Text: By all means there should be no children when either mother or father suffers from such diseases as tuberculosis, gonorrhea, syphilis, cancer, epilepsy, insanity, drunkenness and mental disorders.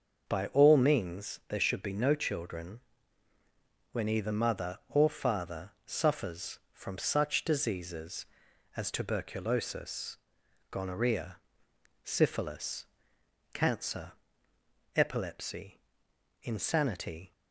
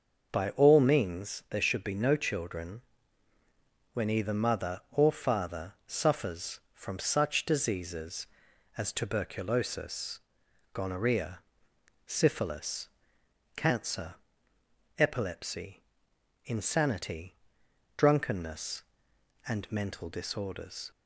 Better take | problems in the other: second | starts louder than the rest; until 1.3 s; 6.5 dB; also in the second // pauses between "children" and "when"; at 2.8 s; 1.1 s long; also in the second // stops before "drunkenness and mental disorders"; at 17.3 s

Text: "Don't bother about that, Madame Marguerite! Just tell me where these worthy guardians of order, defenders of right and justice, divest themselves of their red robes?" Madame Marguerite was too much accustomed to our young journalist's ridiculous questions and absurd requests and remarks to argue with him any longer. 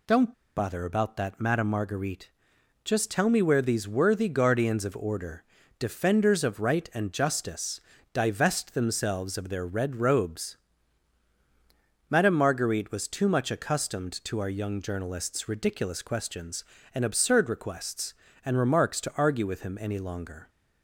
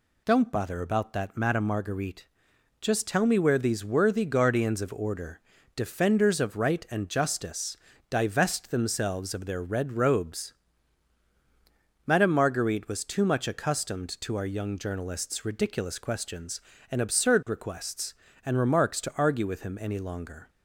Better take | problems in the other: second | pauses between "Don't" and "bother"; slight; at 0.3 s; 0.23 s long

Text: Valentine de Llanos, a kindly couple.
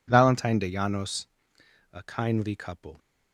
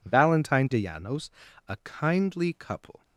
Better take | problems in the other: neither | none

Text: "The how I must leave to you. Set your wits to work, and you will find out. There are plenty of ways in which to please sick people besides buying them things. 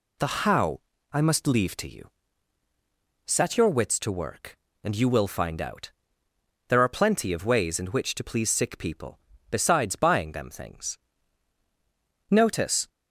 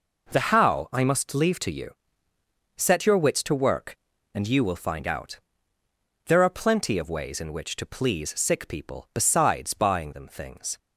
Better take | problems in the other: second | pauses between "how" and "I"; slight; at 0.7 s; 0.32 s long // pauses between "people" and "besides"; slight; at 9.1 s; 0.32 s long // goes on to say "Notice"; from 12.2 s on; 0.58 s long

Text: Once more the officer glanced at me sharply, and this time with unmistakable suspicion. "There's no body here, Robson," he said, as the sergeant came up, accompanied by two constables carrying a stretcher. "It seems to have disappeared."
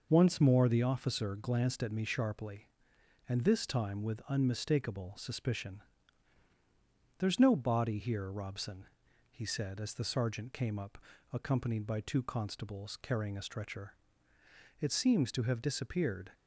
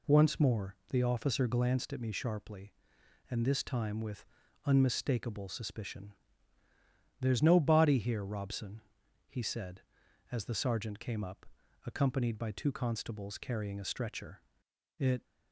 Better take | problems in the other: first | pauses between "more" and "the"; slight; at 0.7 s; 0.16 s long // pauses between "with" and "unmistakable"; at 4.2 s; 0.40 s long // stops before "seems to have disappeared"; at 15.2 s

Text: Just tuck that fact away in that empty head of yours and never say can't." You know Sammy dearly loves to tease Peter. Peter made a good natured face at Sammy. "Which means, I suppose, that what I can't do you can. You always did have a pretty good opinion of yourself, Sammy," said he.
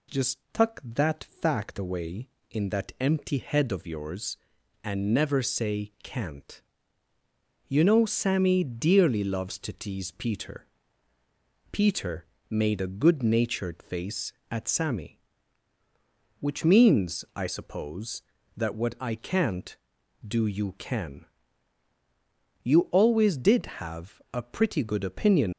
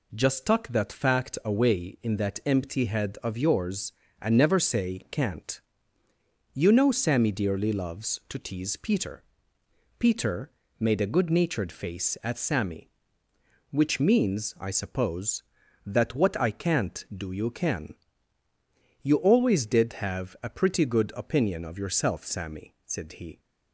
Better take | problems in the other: second | pauses between "Peter" and "made"; slight; at 12.2 s; 0.24 s long; slight in the second // stops before "of yourself Sammy said he"; at 25.5 s

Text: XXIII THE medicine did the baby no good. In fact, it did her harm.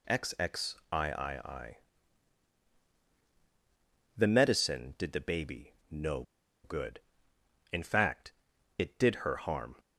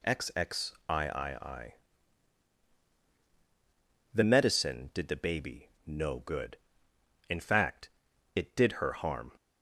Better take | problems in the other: second | pauses between "XXIII" and "THE"; strong; at 1.7 s; 2.4 s long; strong in the second // pauses between "baby" and "no"; slight; at 5.7 s; 0.18 s long; slight in the second // pauses between "no" and "good"; at 6.2 s; 0.40 s long

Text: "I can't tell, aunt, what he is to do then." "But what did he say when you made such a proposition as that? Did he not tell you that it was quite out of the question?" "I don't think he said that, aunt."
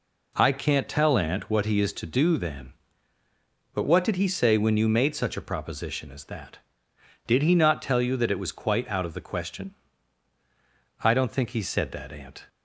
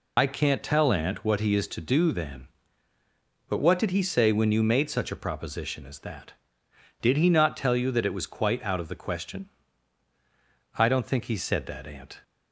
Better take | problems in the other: first | loses the start of "I"; at 0.1 s; 75 ms

